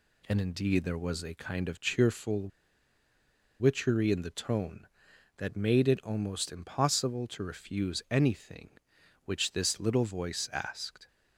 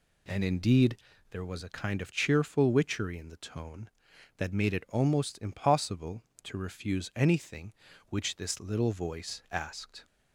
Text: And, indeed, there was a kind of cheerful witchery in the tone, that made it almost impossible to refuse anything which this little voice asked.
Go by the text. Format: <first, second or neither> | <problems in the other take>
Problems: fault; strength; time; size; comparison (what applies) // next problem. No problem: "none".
second | pauses between "cheerful" and "witchery"; at 2.4 s; 1.1 s long